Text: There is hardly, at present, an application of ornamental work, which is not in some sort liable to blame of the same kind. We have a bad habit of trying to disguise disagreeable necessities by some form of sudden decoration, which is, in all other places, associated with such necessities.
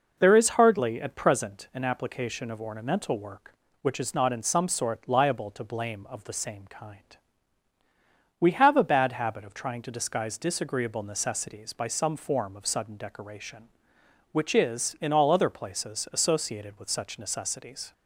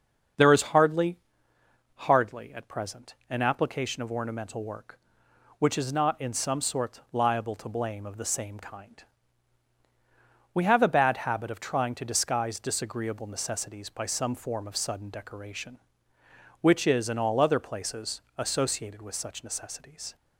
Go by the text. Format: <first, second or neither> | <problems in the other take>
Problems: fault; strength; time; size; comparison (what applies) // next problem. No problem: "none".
first | starts louder than the rest; until 2.1 s; 6.5 dB // says "hardly" twice; at 1.9 s